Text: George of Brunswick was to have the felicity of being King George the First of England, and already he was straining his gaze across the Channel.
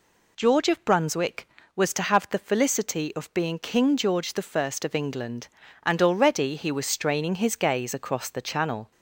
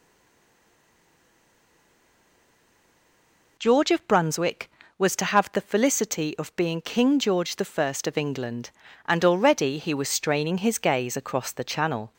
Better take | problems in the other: first | stays silent before the first word; strong; until 3.5 s; 3.5 s long

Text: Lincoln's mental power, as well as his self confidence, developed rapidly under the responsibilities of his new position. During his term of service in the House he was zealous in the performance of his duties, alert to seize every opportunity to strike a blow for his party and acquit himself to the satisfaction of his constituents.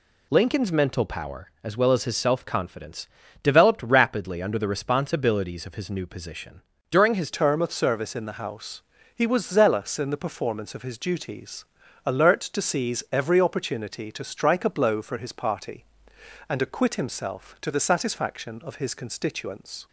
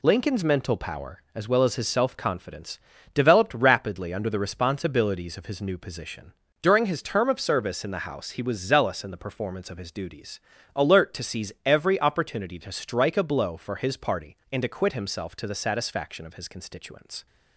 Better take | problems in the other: second | changes voice at "term"; from 7.3 s on; 12.5 s long // pauses between "House" and "he"; slight; at 8.8 s; 0.32 s long

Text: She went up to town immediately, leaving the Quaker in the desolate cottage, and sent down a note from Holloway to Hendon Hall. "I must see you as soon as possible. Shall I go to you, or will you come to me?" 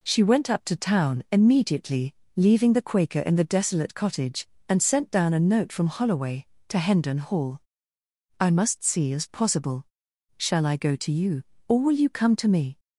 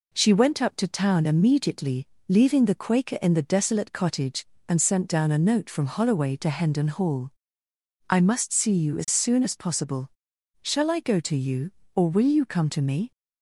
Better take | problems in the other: second | skips "you as soon"; at 9.1 s

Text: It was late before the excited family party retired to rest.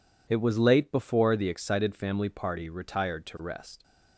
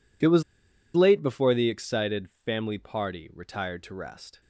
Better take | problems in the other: first | pauses between "was" and "late"; noticeable; at 0.4 s; 0.53 s long

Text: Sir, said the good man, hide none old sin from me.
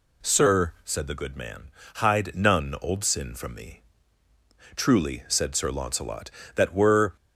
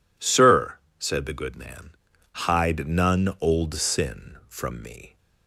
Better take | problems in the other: second | goes on to say "Truly said Sir Launcelot that were"; strong; from 4.7 s on; 2.3 s long

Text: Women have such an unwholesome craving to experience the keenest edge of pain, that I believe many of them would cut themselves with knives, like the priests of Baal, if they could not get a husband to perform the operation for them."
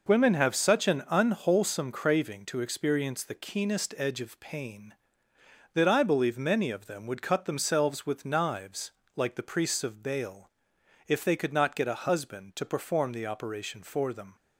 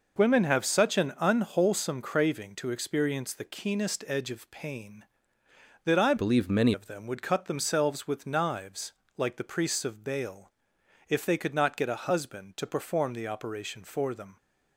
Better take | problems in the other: first | changes voice from "believe" to "many"; from 6.1 to 6.7 s; 0.6 s long

